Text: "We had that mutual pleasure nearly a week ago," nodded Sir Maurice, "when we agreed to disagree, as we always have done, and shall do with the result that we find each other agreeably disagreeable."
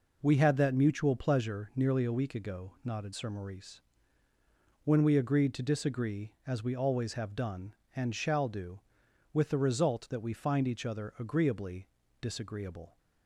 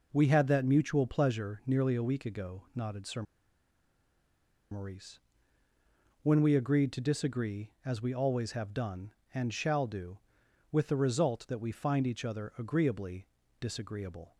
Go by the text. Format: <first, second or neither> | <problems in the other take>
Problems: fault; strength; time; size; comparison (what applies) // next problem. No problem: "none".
first | pauses between "Sir" and "Maurice"; strong; at 3.2 s; 1.4 s long // pauses between "agreeably" and "disagreeable"; slight; at 13.2 s; 0.32 s long; slight in the first